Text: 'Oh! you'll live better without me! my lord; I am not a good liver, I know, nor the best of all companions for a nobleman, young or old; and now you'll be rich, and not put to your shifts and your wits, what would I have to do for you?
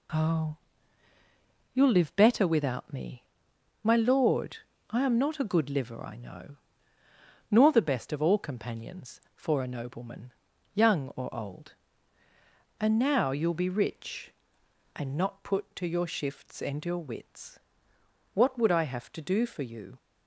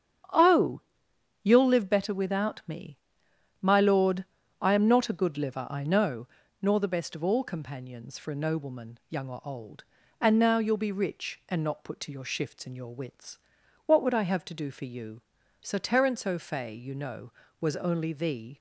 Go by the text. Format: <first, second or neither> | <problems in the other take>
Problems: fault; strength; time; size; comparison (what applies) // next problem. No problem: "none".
first | starts louder than the rest; strong; until 1.9 s; 8 dB // goes on to say "Sir Terence O'Fay you know was only THE"; strong; from 15.6 s on; 2.9 s long